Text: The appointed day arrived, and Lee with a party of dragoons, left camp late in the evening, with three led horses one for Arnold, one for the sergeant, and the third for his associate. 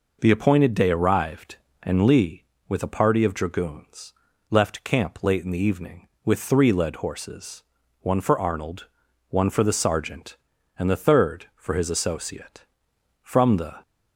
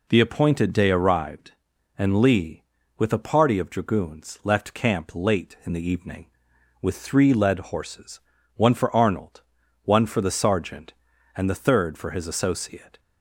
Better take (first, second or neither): second